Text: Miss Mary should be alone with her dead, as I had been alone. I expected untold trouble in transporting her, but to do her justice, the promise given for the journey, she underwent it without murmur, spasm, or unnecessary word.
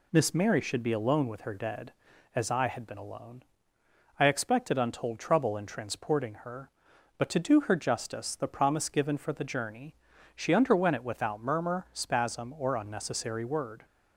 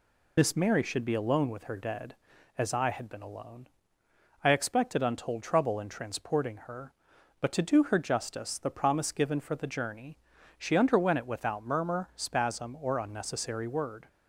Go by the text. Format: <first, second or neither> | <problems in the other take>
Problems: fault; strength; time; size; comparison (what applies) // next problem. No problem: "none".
first | loses the start of "Miss"; at 0.3 s; 40 ms